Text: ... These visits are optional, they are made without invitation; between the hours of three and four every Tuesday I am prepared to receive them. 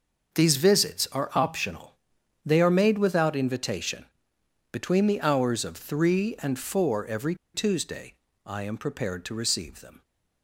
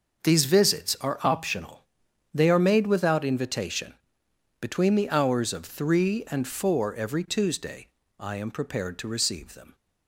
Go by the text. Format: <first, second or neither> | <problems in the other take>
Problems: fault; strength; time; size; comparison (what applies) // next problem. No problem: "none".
second | starts louder than the rest; until 1.4 s; 6.5 dB; also in the second // pauses between "every" and "Tuesday"; slight; at 7.3 s; 0.19 s long // pauses between "Tuesday" and "I"; slight; at 8.1 s; 0.32 s long; slight in the second